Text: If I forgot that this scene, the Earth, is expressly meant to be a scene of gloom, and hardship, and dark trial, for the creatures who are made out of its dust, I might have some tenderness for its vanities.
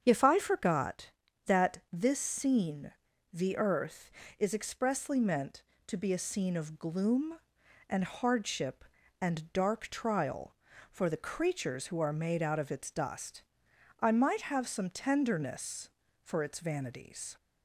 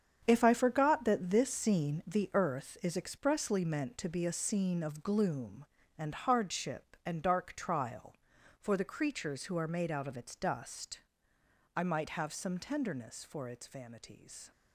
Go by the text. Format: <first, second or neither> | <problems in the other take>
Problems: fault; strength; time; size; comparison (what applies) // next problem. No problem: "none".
first | gets quieter; strong; throughout; 10.5 dB // starts louder than the rest; strong; until 1.2 s; 8 dB; strong in the first